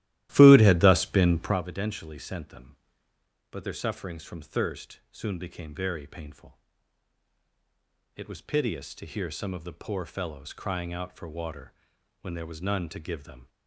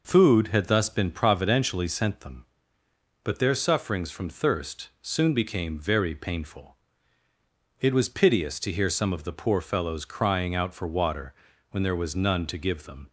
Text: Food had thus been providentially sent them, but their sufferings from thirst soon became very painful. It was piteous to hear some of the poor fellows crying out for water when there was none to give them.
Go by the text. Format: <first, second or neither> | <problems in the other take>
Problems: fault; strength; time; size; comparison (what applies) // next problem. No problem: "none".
second | starts louder than the rest; strong; until 1.6 s; 14.5 dB // pauses between "water" and "when"; noticeable; at 11.7 s; 0.48 s long; also in the second